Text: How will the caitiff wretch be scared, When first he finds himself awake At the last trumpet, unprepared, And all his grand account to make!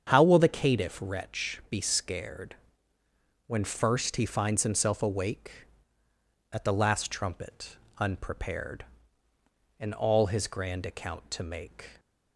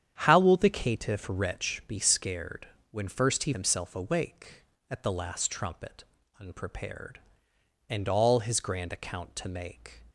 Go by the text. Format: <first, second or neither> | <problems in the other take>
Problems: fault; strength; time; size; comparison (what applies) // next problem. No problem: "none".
first | starts louder than the rest; strong; until 1.2 s; 9 dB; strong in the first // skips "finds"; at 3.5 s